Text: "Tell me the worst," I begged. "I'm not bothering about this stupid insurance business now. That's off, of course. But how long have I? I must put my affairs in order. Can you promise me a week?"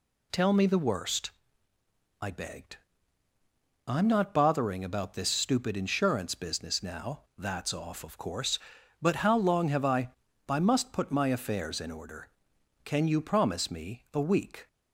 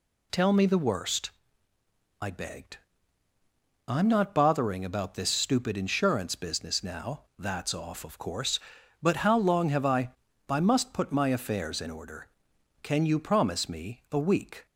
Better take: neither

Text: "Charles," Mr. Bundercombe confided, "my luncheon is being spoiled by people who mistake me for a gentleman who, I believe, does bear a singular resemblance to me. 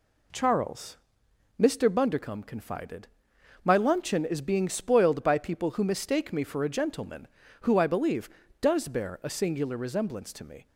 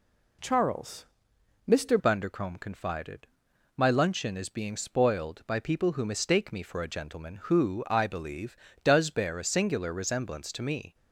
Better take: first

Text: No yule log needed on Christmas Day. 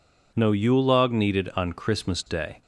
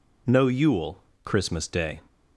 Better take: first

